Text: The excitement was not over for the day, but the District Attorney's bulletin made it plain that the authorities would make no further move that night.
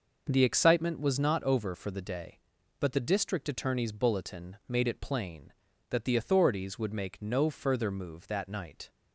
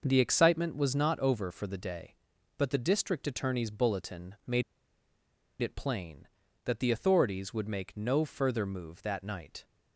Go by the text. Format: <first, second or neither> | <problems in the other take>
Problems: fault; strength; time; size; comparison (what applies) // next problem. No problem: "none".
first | starts louder than the rest; noticeable; until 1.0 s; 6 dB // pauses between "made" and "it"; at 4.6 s; 0.99 s long